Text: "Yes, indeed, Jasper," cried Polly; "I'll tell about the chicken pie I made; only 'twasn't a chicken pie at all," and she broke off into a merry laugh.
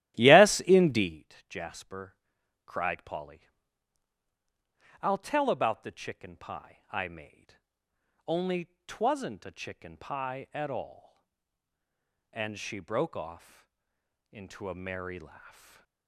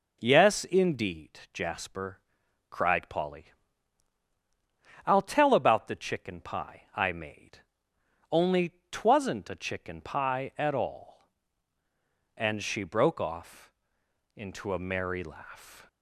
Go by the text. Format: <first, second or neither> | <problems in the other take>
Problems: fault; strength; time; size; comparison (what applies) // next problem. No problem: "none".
second | starts louder than the rest; strong; until 1.3 s; 14 dB // pauses between "off" and "into"; noticeable; at 13.6 s; 0.64 s long; noticeable in the second // stays silent after the last word; slight; from 15.4 s on; 0.6 s long